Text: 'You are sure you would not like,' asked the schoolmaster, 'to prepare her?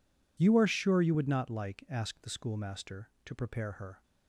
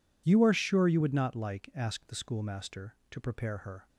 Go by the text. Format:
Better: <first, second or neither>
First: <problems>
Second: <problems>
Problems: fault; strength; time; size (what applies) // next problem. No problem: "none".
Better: neither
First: none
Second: none